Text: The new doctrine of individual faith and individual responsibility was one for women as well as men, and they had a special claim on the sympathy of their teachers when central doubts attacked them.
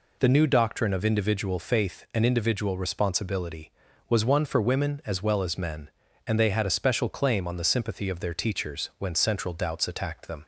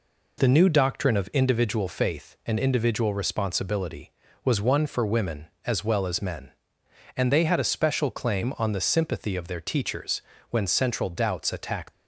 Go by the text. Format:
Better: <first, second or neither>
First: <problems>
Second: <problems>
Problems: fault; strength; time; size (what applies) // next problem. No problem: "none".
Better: first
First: none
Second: pauses between "teachers" and "when"; slight; at 10.2 s; 0.28 s long // stops before "them"; at 11.9 s